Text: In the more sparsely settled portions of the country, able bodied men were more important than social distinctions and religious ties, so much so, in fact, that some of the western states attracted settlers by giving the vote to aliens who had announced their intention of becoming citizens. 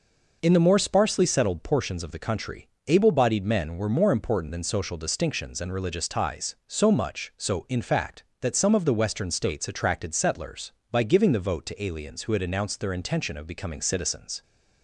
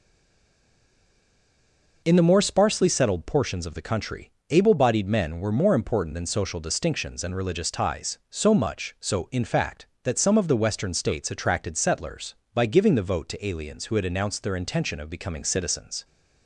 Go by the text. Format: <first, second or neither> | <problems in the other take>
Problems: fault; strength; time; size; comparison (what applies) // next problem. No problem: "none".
first | stays silent before the first word; noticeable; until 2.0 s; 2.0 s long